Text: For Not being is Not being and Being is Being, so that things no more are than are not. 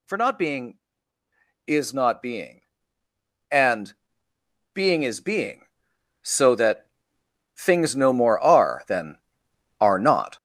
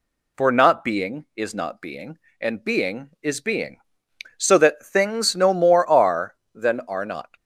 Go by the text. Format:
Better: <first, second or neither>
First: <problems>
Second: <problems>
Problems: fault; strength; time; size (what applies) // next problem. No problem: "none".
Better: second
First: gets louder; strong; throughout; 11 dB // pauses between "and" and "Being"; noticeable; at 3.9 s; 0.84 s long // pauses between "that" and "things"; noticeable; at 6.8 s; 0.70 s long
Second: none